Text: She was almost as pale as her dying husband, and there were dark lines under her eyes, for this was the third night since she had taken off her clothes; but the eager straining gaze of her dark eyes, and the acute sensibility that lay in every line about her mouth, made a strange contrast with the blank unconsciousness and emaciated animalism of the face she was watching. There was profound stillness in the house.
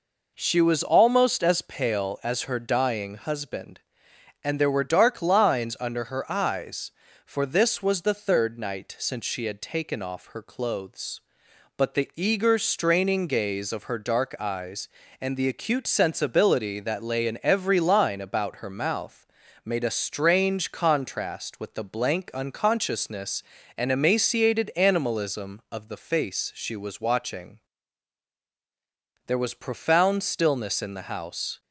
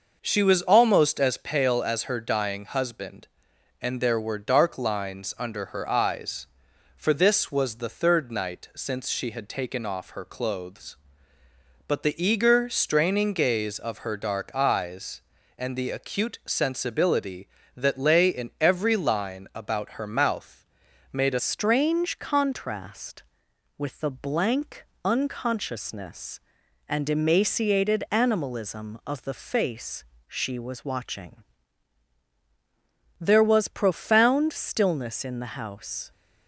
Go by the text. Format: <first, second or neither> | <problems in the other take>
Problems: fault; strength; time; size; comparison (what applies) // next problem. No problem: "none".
first | changes voice at "strange"; from 21.3 s on; 14.8 s long // pauses between "blank" and "unconsciousness"; slight; at 24.8 s; 0.20 s long // pauses between "face" and "she"; slight; at 30.0 s; 0.24 s long